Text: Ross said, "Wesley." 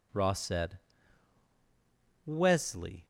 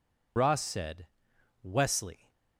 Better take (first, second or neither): first